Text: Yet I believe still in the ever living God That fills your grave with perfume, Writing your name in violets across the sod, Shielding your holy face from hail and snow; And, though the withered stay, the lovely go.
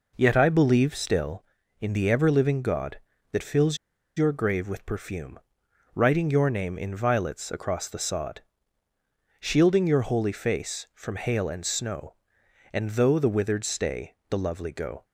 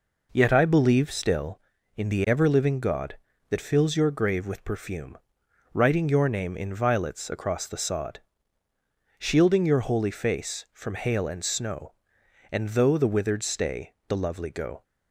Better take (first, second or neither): second